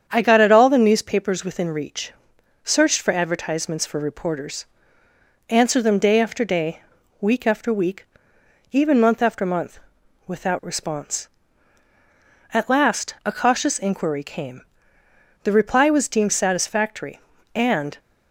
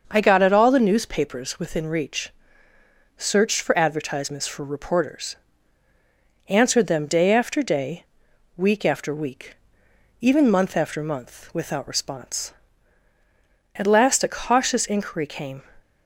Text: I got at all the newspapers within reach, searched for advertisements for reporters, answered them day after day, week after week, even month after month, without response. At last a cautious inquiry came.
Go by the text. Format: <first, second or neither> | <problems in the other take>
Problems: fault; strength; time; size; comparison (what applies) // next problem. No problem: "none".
second | starts louder than the rest; strong; until 1.0 s; 8 dB; also in the second // goes on to say "The reply was deemed satisfactory and"; strong; from 15.4 s on; 2.5 s long